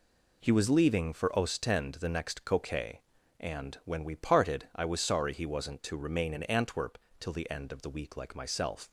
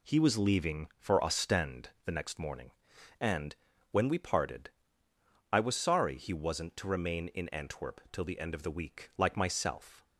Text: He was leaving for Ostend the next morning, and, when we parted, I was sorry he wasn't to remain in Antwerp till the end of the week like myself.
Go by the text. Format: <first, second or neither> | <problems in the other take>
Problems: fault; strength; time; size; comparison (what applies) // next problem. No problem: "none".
second | says "coquet" for "morning"; at 2.4 s // pauses between "Antwerp" and "till"; slight; at 6.9 s; 0.22 s long